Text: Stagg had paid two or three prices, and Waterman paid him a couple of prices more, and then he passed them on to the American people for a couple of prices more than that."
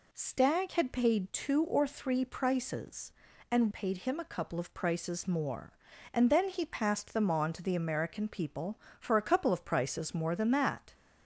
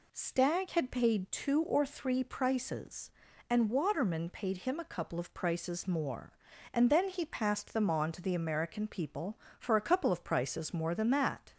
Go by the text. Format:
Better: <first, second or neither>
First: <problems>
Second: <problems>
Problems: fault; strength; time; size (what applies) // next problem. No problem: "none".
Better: second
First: skips "Waterman"; at 3.7 s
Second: none